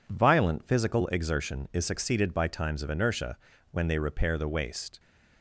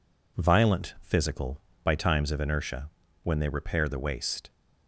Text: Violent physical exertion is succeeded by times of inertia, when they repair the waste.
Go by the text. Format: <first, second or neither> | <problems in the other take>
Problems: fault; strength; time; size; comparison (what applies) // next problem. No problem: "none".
first | skips "exertion is succeeded"; at 1.7 s